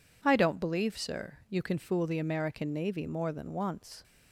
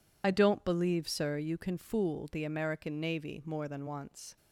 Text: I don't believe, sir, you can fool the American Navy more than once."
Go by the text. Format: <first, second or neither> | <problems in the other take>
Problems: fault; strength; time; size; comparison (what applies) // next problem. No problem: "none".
first | loses the start of "I"; at 0.2 s; 50 ms